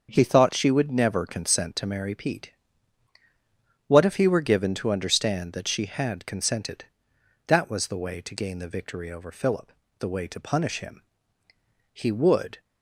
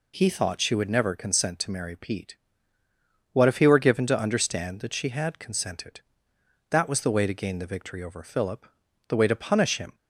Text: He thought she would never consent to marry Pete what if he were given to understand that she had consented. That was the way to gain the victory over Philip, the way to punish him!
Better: second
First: starts louder than the rest; until 1.1 s; 6.5 dB // pauses between "Pete" and "what"; strong; at 2.5 s; 1.3 s long // goes on to say "He would"; noticeable; from 11.9 s on; 0.68 s long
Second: pauses between "Pete" and "what"; noticeable; at 2.3 s; 0.96 s long

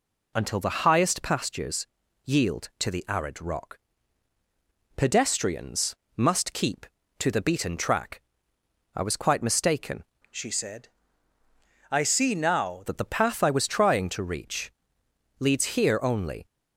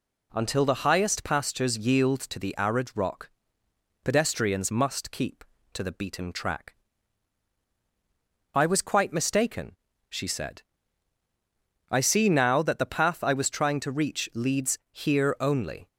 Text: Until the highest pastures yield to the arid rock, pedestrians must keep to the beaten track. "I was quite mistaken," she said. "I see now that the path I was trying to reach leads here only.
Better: second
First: pauses between "pastures" and "yield"; at 1.8 s; 0.38 s long // pauses between "pedestrians" and "must"; slight; at 5.9 s; 0.20 s long // changes voice from "she" to "now"; from 10.2 to 12.8 s; 2.6 s long // pauses between "reach" and "leads"; noticeable; at 14.7 s; 0.68 s long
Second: none

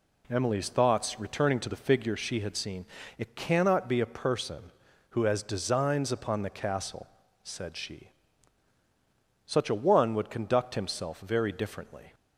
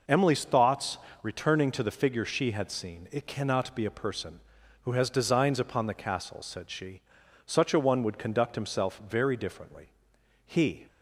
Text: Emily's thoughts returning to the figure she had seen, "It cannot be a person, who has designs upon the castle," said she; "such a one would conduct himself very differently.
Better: first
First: none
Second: pauses between "thoughts" and "returning"; slight; at 0.9 s; 0.24 s long // goes on to say "He"; slight; from 10.4 s on; 0.42 s long

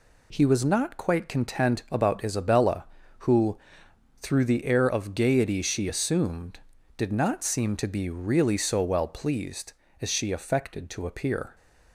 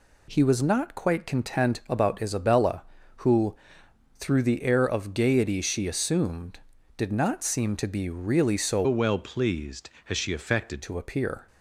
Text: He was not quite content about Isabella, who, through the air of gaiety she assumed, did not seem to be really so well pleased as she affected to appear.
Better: first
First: none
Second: changes voice from "well" to "affected"; from 8.8 to 10.8 s; 2.0 s long

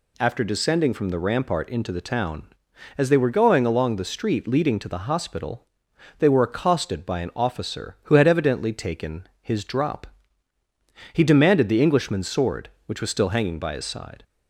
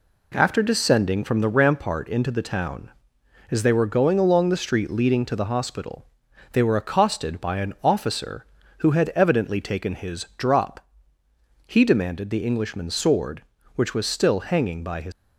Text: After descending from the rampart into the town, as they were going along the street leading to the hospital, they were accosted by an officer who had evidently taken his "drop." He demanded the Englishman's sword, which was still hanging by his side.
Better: first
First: none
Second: stops before "side"; at 15.1 s

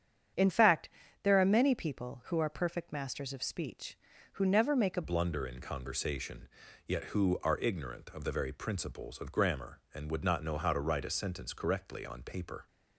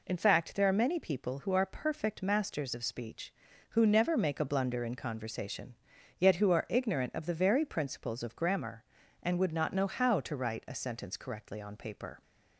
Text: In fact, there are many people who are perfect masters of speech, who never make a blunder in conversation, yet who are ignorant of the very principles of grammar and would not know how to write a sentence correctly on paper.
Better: second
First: starts louder than the rest; strong; until 1.6 s; 8.5 dB // changes voice at "blunder"; from 5.0 s on; 7.6 s long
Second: none

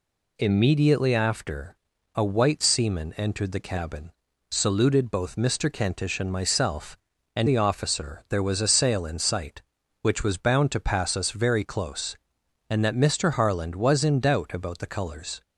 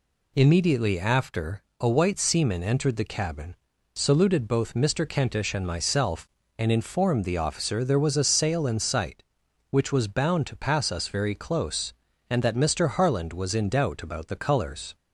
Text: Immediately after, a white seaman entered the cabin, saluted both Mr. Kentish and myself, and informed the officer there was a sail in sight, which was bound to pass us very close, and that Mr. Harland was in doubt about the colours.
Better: second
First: skips "informed"; at 7.4 s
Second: none

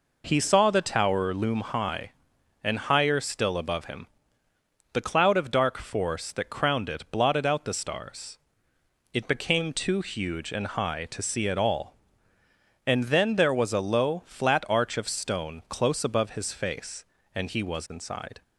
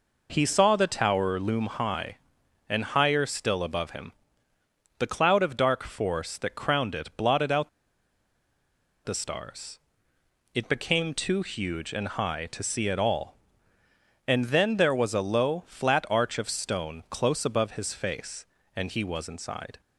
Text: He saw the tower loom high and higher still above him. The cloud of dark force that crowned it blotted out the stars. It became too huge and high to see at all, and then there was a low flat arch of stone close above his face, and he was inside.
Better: first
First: none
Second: pauses between "out" and "the"; strong; at 7.6 s; 1.3 s long

